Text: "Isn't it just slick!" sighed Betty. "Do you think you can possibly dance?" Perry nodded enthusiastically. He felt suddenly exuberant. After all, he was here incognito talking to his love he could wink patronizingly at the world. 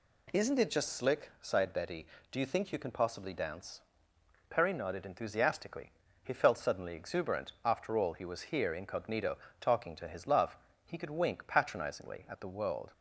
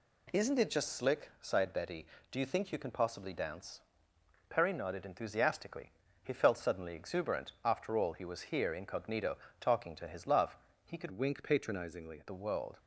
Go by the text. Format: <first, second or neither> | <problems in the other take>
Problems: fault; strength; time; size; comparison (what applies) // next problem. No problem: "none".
first | pauses between "incognito" and "talking"; slight; at 9.3 s; 0.20 s long; slight in the first // pauses between "love" and "he"; slight; at 10.5 s; 0.30 s long; slight in the first // changes voice from "wink" to "at"; from 11.1 to 12.2 s; 1.1 s long